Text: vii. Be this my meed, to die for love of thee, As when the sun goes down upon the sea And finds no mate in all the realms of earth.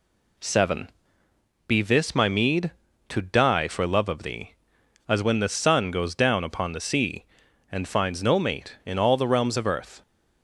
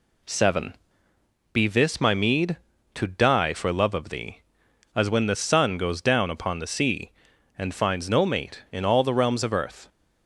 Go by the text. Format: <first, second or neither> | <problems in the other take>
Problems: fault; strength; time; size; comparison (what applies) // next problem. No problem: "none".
neither | none